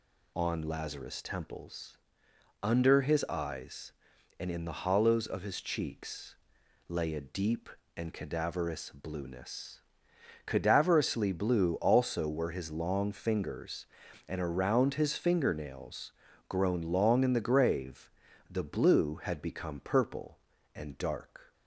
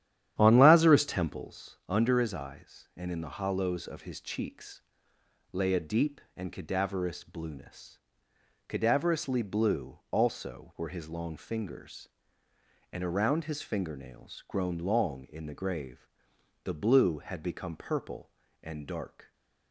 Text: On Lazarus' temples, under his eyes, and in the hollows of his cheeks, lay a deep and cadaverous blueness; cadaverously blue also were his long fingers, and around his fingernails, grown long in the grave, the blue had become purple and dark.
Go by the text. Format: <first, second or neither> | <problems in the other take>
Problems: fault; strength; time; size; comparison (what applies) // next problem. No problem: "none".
first | starts louder than the rest; strong; until 1.5 s; 11 dB